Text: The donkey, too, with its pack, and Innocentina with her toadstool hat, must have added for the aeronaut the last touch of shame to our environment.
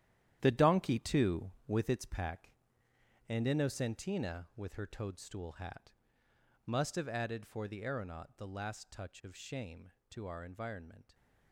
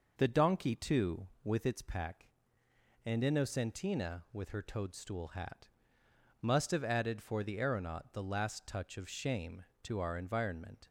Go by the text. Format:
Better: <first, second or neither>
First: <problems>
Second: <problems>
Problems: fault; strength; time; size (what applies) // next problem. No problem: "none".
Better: second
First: gets quieter; strong; throughout; 11.5 dB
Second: none